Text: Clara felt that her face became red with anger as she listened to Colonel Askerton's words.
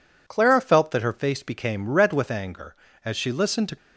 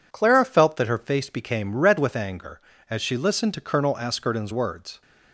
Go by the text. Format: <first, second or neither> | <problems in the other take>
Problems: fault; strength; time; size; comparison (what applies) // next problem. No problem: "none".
second | stops before "Colonel Askerton's words"; at 3.7 s